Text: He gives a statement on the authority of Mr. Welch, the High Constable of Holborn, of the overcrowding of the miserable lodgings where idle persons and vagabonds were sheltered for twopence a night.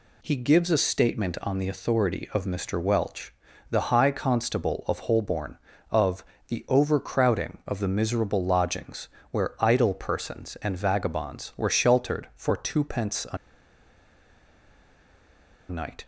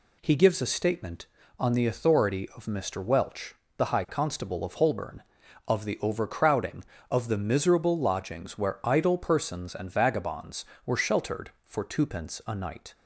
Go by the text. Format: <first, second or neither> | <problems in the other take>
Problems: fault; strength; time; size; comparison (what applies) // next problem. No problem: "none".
second | pauses between "of" and "the"; slight; at 6.2 s; 0.24 s long // pauses between "lodgings" and "where"; slight; at 9.0 s; 0.24 s long // pauses between "a" and "night"; strong; at 13.3 s; 2.3 s long